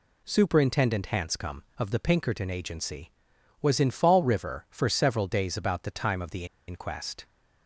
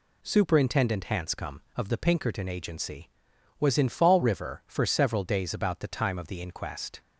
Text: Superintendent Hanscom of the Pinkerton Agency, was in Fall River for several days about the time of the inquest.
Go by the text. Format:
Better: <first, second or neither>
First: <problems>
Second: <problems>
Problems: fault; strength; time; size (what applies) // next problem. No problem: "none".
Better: second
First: pauses between "the" and "inquest"; slight; at 6.4 s; 0.23 s long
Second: none